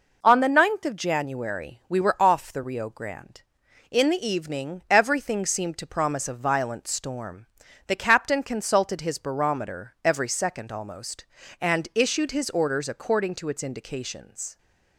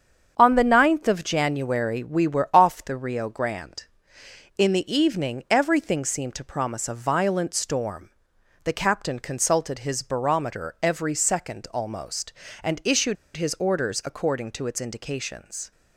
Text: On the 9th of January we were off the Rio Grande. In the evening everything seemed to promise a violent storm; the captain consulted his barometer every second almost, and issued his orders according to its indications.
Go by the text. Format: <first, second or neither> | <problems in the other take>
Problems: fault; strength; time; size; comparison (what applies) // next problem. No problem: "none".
first | starts louder than the rest; strong; until 1.3 s; 7.5 dB // pauses between "issued" and "his"; slight; at 13.1 s; 0.21 s long